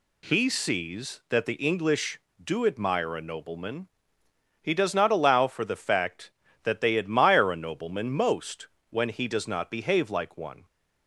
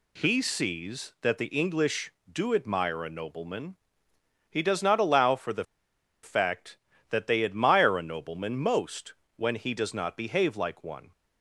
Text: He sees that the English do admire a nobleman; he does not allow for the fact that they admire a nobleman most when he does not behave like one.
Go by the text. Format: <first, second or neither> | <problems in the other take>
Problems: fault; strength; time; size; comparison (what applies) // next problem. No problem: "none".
first | pauses between "the" and "fact"; noticeable; at 5.6 s; 0.60 s long // pauses between "most" and "when"; slight; at 9.1 s; 0.24 s long; slight in the first